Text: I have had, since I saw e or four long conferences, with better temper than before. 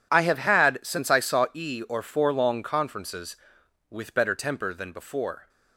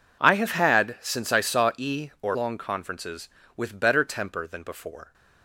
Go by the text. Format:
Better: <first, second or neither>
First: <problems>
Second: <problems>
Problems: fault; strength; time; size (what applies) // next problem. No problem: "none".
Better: first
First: none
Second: skips "four"; at 2.3 s